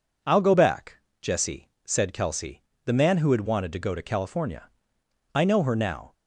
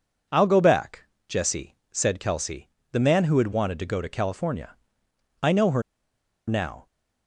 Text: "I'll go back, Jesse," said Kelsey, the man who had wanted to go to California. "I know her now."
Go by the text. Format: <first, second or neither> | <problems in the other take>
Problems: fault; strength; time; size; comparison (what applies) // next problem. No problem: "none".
first | pauses between "her" and "now"; noticeable; at 5.8 s; 0.67 s long